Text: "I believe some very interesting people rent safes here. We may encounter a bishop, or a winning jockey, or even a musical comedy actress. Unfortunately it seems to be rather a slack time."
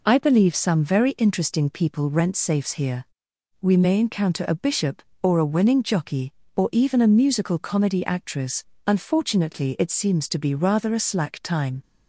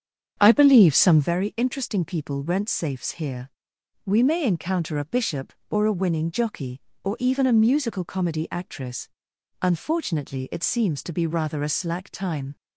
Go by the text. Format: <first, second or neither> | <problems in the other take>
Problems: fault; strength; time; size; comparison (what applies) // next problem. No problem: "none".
first | starts louder than the rest; strong; until 1.3 s; 7.5 dB